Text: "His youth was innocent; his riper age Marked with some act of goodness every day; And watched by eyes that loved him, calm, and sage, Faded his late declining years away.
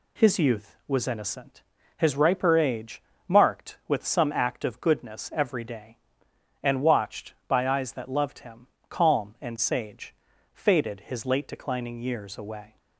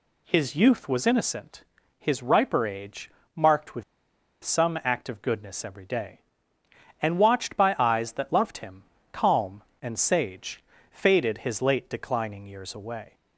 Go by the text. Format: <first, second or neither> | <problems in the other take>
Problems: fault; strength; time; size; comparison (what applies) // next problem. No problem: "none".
first | pauses between "age" and "Marked"; slight; at 3.1 s; 0.26 s long; slight in the first // pauses between "with" and "some"; noticeable; at 3.8 s; 0.60 s long